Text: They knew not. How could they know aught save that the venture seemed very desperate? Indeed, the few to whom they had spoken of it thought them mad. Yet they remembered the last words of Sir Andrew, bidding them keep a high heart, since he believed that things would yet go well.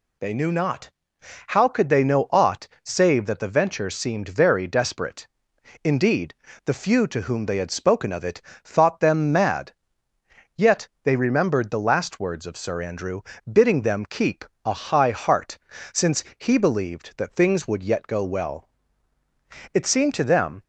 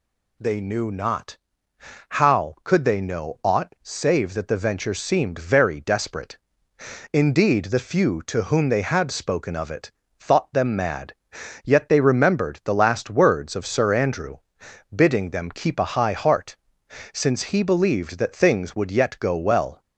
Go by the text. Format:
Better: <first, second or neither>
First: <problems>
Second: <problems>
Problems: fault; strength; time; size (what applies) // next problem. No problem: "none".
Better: second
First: pauses between "aught" and "save"; slight; at 2.6 s; 0.16 s long // pauses between "it" and "thought"; slight; at 8.4 s; 0.22 s long // pauses between "Yet" and "they"; slight; at 10.8 s; 0.16 s long // pauses between "keep" and "a"; slight; at 14.4 s; 0.20 s long // pauses between "since" and "he"; slight; at 16.2 s; 0.16 s long // goes on to say "It seemed to them"; noticeable; from 19.7 s on; 0.90 s long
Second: pauses between "it" and "thought"; slight; at 9.9 s; 0.28 s long